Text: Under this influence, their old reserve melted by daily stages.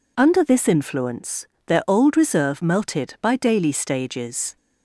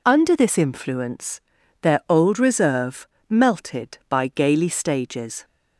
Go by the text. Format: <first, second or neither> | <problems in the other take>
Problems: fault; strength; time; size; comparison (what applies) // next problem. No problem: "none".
first | pauses between "reserve" and "melted"; slight; at 3.0 s; 0.22 s long // says "gaily" for "daily"; at 4.2 s